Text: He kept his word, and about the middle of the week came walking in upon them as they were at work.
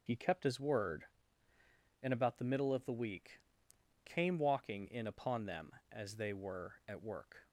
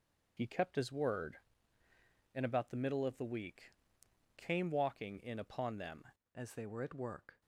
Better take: first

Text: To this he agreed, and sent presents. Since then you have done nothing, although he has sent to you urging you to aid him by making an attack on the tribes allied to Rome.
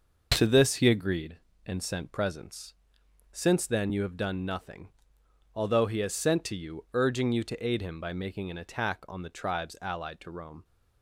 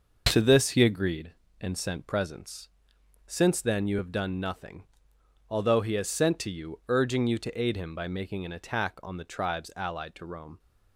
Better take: neither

